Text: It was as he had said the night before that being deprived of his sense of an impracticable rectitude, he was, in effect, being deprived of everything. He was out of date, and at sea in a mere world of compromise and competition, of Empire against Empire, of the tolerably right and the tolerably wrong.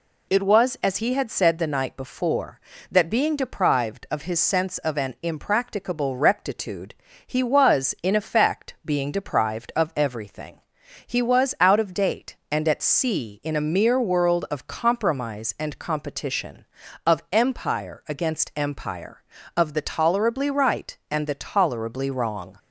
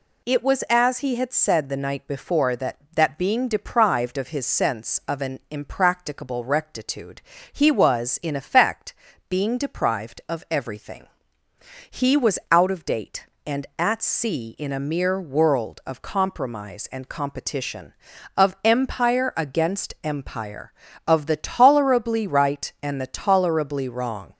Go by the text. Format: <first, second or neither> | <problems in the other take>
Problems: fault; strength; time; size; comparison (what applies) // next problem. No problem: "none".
first | says "that" twice; at 2.9 s